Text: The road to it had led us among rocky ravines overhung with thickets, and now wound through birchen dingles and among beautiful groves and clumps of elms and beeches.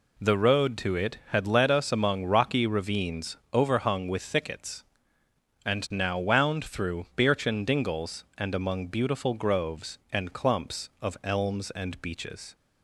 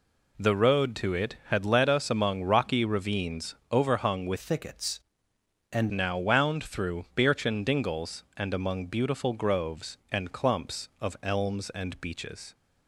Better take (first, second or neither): first